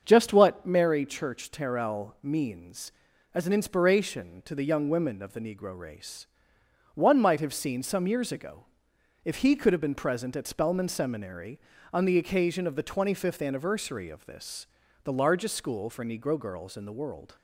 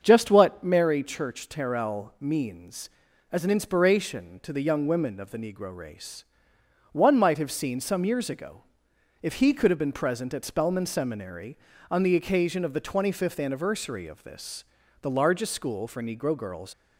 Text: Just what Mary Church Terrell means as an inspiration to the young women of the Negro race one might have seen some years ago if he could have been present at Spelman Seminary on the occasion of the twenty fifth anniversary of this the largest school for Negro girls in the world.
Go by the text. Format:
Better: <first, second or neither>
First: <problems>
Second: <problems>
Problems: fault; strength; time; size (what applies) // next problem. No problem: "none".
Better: first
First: starts louder than the rest; until 1.0 s; 7 dB // pauses between "race" and "one"; noticeable; at 6.2 s; 0.66 s long // pauses between "ago" and "if"; noticeable; at 8.6 s; 0.58 s long // pauses between "this" and "the"; at 14.6 s; 0.38 s long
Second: starts louder than the rest; until 1.0 s; 7 dB // pauses between "race" and "one"; noticeable; at 6.2 s; 0.66 s long // pauses between "ago" and "if"; noticeable; at 8.6 s; 0.58 s long // pauses between "this" and "the"; at 14.6 s; 0.38 s long // stops before "in the world"; at 16.7 s